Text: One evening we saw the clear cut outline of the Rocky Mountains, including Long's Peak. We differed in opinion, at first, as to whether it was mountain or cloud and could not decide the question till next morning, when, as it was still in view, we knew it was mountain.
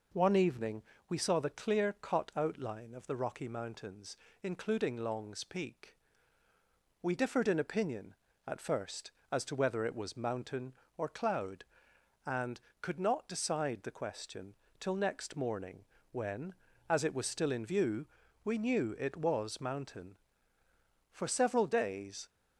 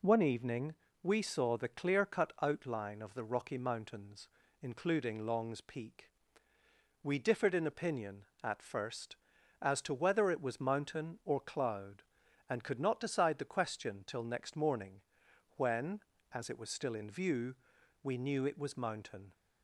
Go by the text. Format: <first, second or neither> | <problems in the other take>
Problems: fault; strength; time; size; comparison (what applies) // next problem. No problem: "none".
second | pauses between "evening" and "we"; slight; at 0.8 s; 0.26 s long; slight in the second // pauses between "question" and "till"; slight; at 14.5 s; 0.26 s long // goes on to say "For several days"; noticeable; from 21.1 s on; 1.1 s long